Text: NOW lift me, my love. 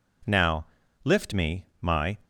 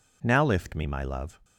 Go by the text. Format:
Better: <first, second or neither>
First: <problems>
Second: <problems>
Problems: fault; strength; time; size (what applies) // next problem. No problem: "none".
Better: second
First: pauses between "NOW" and "lift"; at 0.6 s; 0.40 s long // stops before "love"; at 2.2 s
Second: none